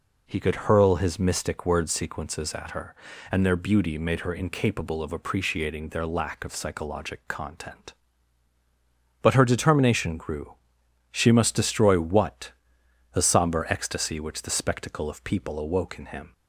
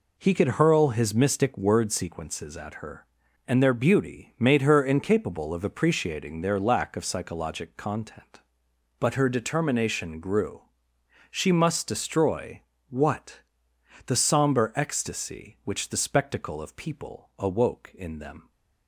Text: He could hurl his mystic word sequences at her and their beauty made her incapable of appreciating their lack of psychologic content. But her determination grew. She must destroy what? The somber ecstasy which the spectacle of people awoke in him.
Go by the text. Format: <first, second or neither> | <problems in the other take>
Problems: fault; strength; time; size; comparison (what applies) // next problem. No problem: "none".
first | pauses between "destroy" and "what"; slight; at 12.6 s; 0.30 s long // says "them" for "him"; at 18.1 s